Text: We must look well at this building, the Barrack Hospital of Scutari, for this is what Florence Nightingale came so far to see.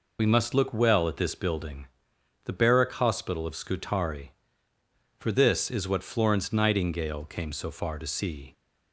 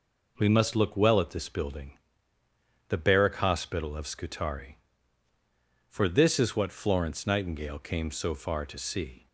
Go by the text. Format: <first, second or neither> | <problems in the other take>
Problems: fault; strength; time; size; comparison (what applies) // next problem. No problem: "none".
second | loses the start of "We"; at 0.1 s; 35 ms